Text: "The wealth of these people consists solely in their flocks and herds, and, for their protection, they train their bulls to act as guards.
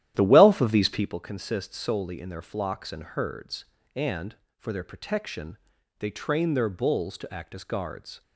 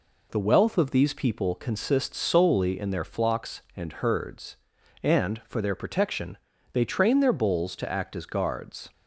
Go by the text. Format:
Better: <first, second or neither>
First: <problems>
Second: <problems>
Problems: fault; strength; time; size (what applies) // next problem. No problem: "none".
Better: second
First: starts louder than the rest; strong; until 1.2 s; 12 dB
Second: none